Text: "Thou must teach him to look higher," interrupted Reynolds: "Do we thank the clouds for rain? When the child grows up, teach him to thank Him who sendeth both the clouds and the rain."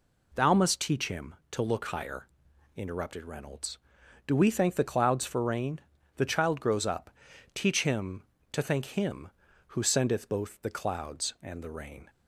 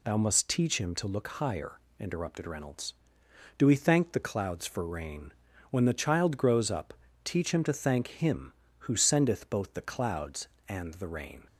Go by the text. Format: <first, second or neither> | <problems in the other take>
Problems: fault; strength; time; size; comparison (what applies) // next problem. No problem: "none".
second | skips "When"; at 5.9 s